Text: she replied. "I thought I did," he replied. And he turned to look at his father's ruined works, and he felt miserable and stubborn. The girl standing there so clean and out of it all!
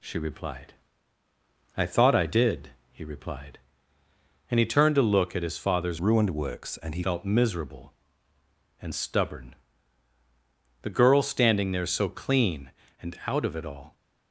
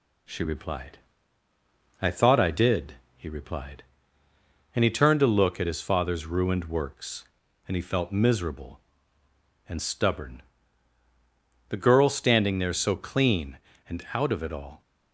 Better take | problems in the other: second | changes voice from "ruined" to "he"; from 5.9 to 7.0 s; 1.1 s long

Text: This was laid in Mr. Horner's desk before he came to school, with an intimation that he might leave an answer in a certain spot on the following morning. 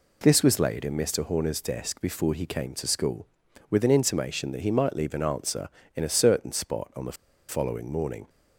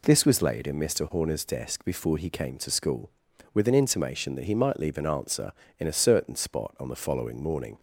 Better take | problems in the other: second | pauses between "the" and "following"; slight; at 7.1 s; 0.34 s long

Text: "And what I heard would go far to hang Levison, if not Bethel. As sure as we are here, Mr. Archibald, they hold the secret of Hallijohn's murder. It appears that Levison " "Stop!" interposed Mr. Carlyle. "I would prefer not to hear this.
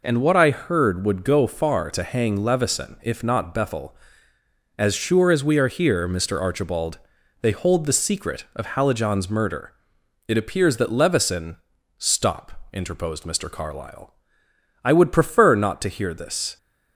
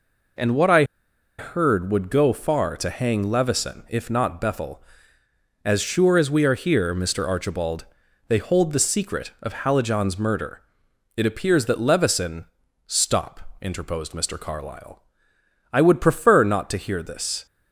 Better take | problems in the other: first | pauses between "I" and "heard"; noticeable; at 0.8 s; 0.55 s long

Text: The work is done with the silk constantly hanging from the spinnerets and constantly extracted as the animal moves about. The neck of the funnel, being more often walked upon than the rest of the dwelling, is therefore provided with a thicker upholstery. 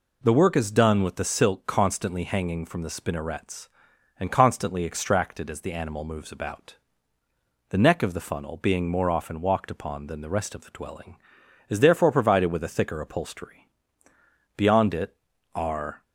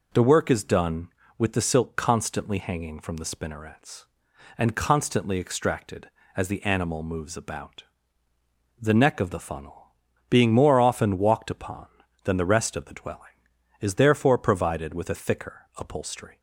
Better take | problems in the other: second | goes on to say "Beyond it are"; from 14.5 s on; 1.4 s long

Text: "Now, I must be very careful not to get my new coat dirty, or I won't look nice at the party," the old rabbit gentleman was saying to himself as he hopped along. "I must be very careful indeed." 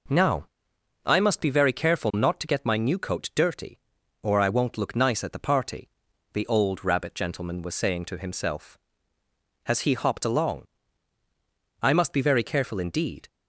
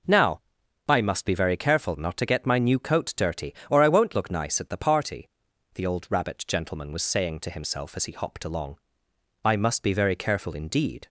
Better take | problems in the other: second | says "has" for "as"; at 9.6 s

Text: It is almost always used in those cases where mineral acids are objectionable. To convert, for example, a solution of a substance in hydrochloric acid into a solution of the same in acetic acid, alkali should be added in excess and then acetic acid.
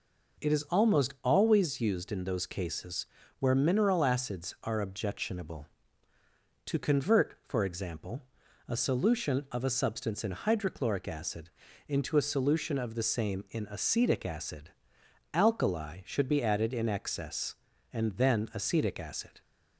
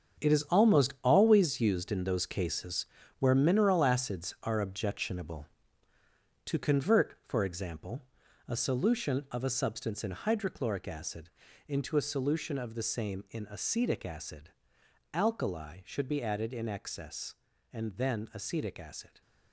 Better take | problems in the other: first | gets quieter; strong; throughout; 11 dB // pauses between "cases" and "where"; slight; at 2.8 s; 0.34 s long; slight in the first // pauses between "acid" and "into"; at 11.2 s; 0.40 s long; also in the first

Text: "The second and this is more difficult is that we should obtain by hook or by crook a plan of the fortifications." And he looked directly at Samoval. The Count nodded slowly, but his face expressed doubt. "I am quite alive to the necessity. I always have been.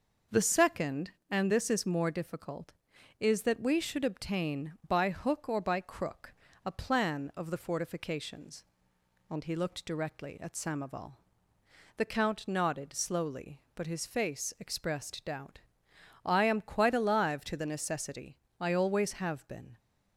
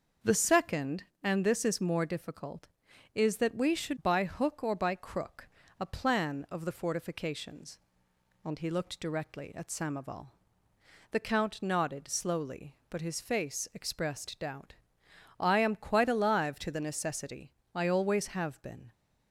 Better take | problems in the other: first | skips "obtain"; at 4.0 s // pauses between "crook" and "a"; slight; at 5.4 s; 0.32 s long; slight in the first

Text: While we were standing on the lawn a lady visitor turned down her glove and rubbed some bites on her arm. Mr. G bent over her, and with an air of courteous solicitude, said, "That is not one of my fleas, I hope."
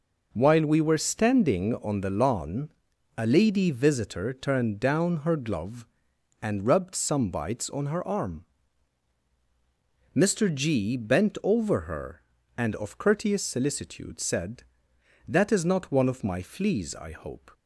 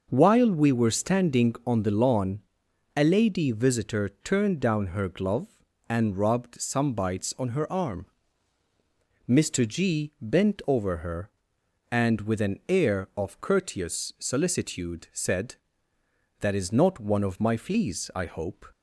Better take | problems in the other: second | pauses between "lawn" and "a"; noticeable; at 2.6 s; 0.48 s long; noticeable in the second // skips "with an air"; at 12.7 s

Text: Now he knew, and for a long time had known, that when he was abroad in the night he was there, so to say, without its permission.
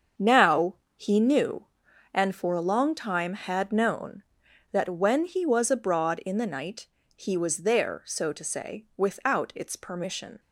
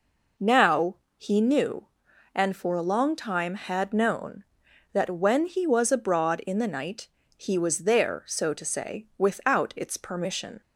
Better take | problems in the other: second | gets quieter; strong; throughout; 9 dB // pauses between "Now" and "he"; slight; at 0.7 s; 0.20 s long; slight in the second // pauses between "night" and "he"; slight; at 6.8 s; 0.30 s long; slight in the second

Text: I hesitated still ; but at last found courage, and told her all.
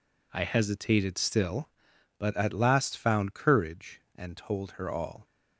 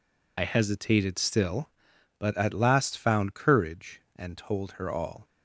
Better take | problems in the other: first | loses the start of "I"; at 0.3 s; 50 ms

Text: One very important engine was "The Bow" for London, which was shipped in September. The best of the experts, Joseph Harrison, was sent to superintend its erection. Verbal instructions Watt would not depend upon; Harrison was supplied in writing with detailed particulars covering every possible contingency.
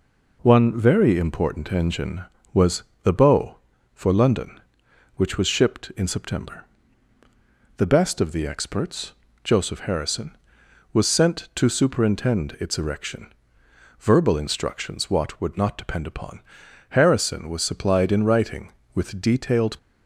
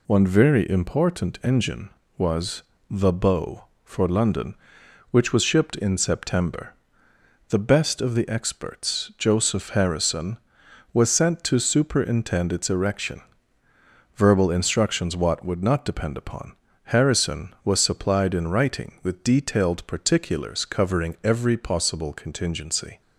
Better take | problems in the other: second | pauses between "was" and "The"; slight; at 2.8 s; 0.18 s long; slight in the second // stops before "particulars covering every possible contingency"; at 19.7 s

